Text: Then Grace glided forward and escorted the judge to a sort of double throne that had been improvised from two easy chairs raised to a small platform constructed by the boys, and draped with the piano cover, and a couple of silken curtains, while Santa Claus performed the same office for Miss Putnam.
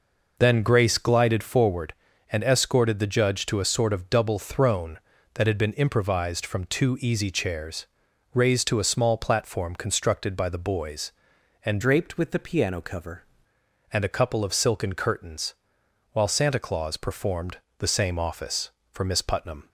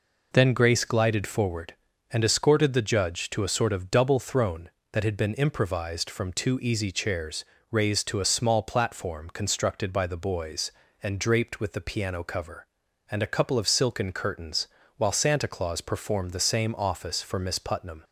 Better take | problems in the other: second | pauses between "chairs" and "raised"; noticeable; at 7.8 s; 0.46 s long; slight in the second // changes voice from "draped" to "cover"; from 11.8 to 13.2 s; 1.4 s long // pauses between "performed" and "the"; slight; at 17.5 s; 0.22 s long

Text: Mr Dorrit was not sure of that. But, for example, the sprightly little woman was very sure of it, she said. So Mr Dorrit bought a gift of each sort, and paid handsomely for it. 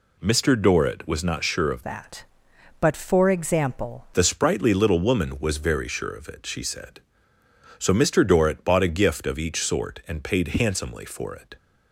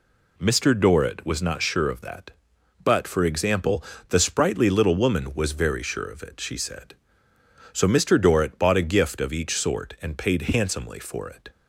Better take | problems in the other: second | changes voice from "that" to "example"; from 1.8 to 4.0 s; 2.2 s long

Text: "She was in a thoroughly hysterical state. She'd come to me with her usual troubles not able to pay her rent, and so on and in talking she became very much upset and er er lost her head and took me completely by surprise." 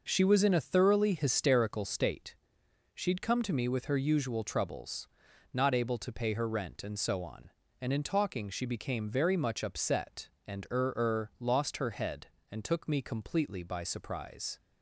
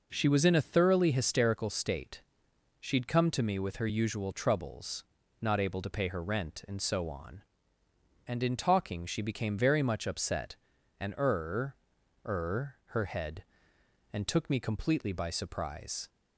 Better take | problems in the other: first | pauses between "troubles" and "not"; slight; at 5.0 s; 0.36 s long; also in the first // pauses between "er" and "er"; noticeable; at 11.7 s; 0.50 s long // skips "lost"; at 12.8 s

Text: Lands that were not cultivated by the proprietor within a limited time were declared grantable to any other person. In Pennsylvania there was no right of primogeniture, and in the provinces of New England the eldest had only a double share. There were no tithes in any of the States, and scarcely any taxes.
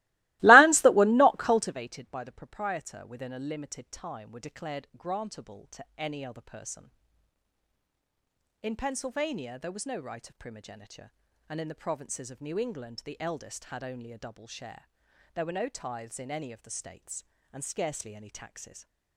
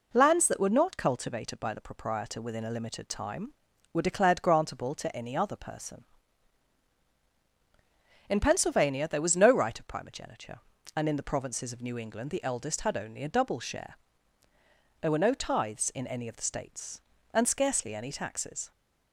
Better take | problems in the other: second | starts louder than the rest; strong; until 1.7 s; 20.5 dB

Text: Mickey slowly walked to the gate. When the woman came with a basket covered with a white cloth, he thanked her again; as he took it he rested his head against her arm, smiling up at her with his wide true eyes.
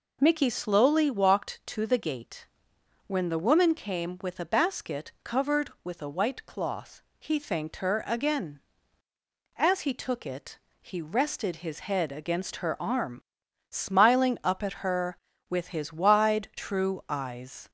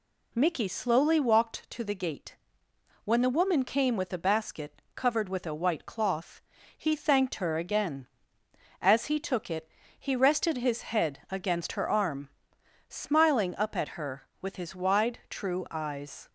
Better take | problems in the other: neither | pauses between "it" and "he"; slight; the same in both

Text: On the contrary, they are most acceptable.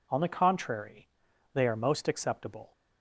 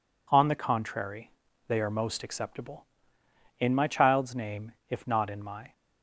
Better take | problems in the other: first | goes on to say "In my child's name if not in my"; strong; from 3.5 s on; 2.1 s long

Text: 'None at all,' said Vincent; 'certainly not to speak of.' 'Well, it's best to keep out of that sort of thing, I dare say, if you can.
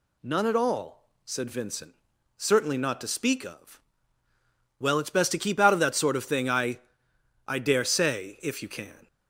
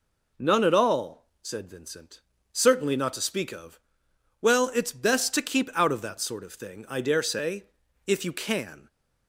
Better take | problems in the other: second | says "I" twice; at 7.4 s

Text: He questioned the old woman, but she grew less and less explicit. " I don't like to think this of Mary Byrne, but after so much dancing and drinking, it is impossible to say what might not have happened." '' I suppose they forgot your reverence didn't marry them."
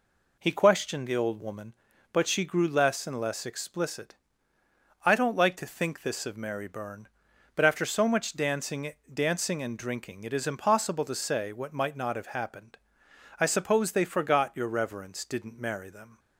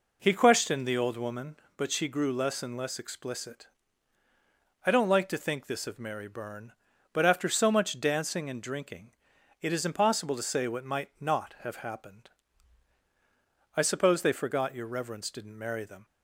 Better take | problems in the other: second | says "dancing" twice; at 9.1 s

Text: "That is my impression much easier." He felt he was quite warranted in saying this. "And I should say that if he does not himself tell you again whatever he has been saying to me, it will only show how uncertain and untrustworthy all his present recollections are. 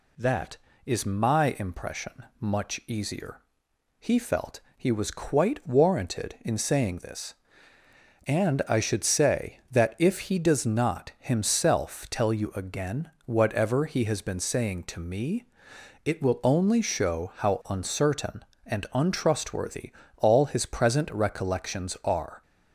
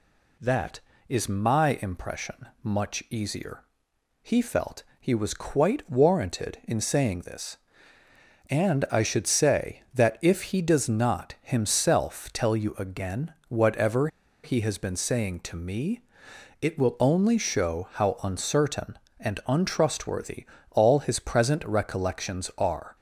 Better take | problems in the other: first | pauses between "felt" and "he"; slight; at 4.8 s; 0.16 s long; slight in the first // pauses between "again" and "whatever"; slight; at 13.3 s; 0.16 s long; slight in the first // pauses between "whatever" and "he"; slight; at 14.0 s; 0.35 s long // pauses between "untrustworthy" and "all"; slight; at 20.4 s; 0.24 s long; slight in the first

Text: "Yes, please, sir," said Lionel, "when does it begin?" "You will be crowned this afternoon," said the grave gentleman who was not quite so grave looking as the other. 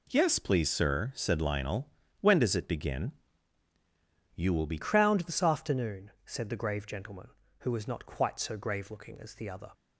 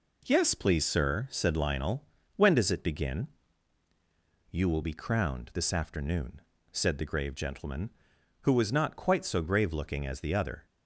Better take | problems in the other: second | changes voice at "crowned"; from 4.7 s on; 5.0 s long

